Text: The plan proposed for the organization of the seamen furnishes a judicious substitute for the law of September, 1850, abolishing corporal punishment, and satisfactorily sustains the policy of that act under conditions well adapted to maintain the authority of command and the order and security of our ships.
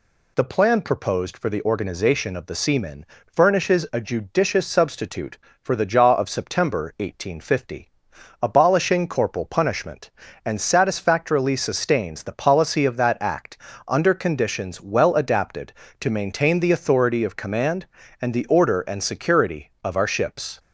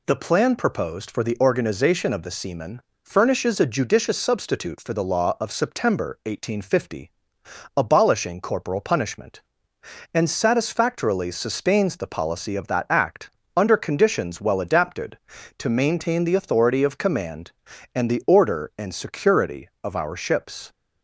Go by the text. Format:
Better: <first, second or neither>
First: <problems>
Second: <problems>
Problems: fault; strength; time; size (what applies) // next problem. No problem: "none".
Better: second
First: pauses between "seamen" and "furnishes"; slight; at 3.0 s; 0.26 s long // says "jaw" for "law"; at 5.8 s // pauses between "act" and "under"; slight; at 13.5 s; 0.30 s long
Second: pauses between "seamen" and "furnishes"; slight; at 2.8 s; 0.24 s long // pauses between "act" and "under"; slight; at 13.3 s; 0.26 s long